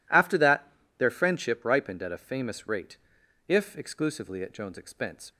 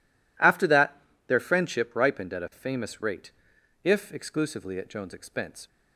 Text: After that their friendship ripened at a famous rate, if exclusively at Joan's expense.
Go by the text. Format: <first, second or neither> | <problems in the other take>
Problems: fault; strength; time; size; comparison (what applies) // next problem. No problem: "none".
neither | pauses between "that" and "their"; slight; the same in both